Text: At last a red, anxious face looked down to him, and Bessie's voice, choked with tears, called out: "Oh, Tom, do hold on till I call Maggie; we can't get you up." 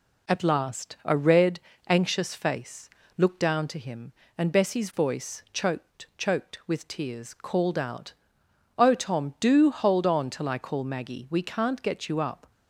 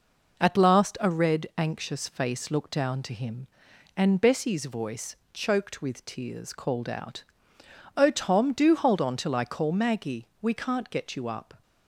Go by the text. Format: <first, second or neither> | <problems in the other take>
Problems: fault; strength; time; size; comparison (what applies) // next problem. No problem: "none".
second | pauses between "face" and "looked"; slight; at 2.8 s; 0.28 s long // says "choked" twice; at 6.1 s